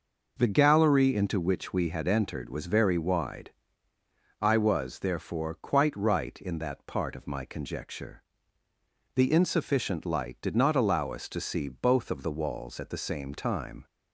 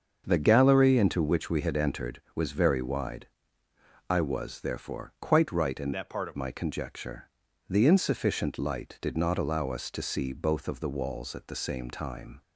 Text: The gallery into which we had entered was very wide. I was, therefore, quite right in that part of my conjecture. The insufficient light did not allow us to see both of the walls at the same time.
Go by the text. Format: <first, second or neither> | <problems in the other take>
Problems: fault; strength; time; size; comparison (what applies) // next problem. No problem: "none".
first | starts louder than the rest; until 1.2 s; 6.5 dB // changes voice from "that" to "of"; from 5.9 to 6.3 s; 0.4 s long